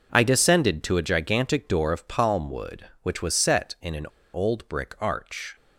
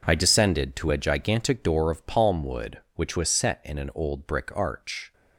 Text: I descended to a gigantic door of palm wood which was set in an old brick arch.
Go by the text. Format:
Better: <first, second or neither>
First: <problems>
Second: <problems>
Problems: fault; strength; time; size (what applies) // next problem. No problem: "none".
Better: second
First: pauses between "an" and "old"; slight; at 4.0 s; 0.26 s long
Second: none